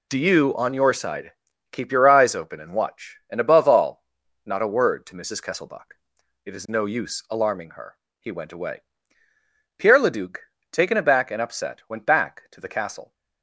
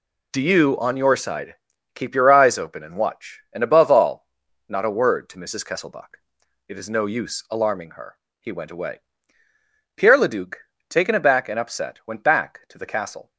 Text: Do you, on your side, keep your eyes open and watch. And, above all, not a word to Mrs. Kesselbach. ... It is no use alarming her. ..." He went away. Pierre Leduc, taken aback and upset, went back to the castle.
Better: neither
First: none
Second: none

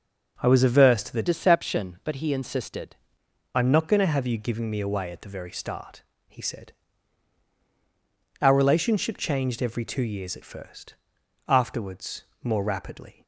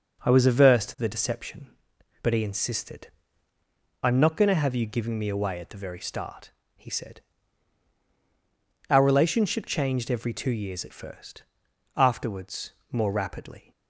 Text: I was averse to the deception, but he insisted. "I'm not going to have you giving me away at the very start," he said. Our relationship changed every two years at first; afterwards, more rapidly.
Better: second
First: starts louder than the rest; until 1.4 s; 6 dB // changes voice from "deception" to "insisted"; from 1.2 to 2.9 s; 1.7 s long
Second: none

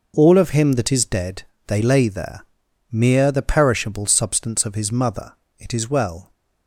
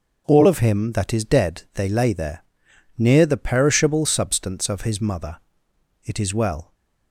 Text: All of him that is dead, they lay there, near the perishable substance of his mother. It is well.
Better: second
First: says "mere" for "near"; at 2.9 s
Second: none

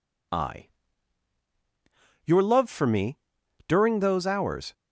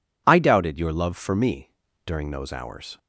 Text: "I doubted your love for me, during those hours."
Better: second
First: skips "doubted"; at 1.4 s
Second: none

